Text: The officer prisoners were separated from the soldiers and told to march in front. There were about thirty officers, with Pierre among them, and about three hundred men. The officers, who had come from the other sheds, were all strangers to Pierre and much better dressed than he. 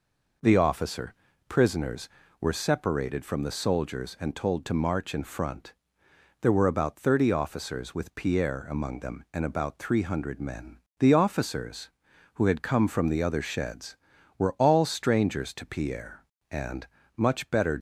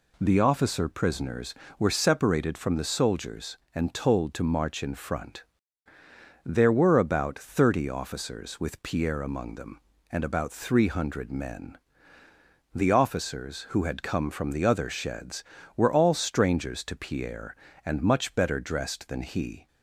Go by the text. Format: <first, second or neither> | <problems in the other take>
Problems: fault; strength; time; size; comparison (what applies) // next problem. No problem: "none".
second | pauses between "officer" and "prisoners"; slight; at 1.1 s; 0.34 s long // pauses between "and" and "much"; slight; at 16.8 s; 0.30 s long // stops before "dressed than he"; at 17.7 s